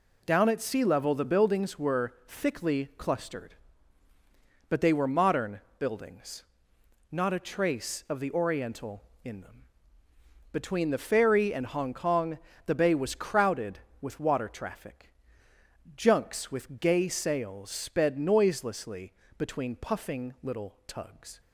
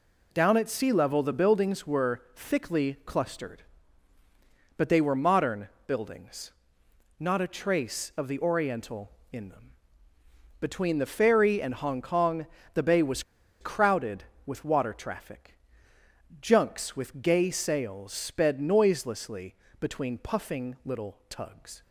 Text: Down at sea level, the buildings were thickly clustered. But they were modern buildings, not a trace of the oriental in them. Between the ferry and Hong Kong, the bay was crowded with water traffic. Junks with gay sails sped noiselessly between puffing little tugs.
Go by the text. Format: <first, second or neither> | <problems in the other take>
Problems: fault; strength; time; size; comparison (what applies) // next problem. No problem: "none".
first | pauses between "modern" and "buildings"; slight; at 5.6 s; 0.18 s long; slight in the first // pauses between "was" and "crowded"; at 13.2 s; 0.37 s long // pauses between "noiselessly" and "between"; slight; at 19.5 s; 0.26 s long; slight in the first